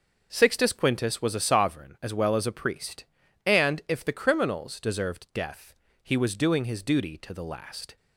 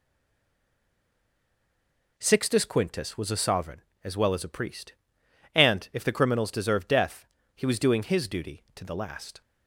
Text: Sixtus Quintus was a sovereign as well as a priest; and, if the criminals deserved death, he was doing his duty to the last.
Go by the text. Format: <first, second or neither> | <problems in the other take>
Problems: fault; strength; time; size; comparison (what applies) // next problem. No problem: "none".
first | stays silent before the first word; until 2.1 s; 2.1 s long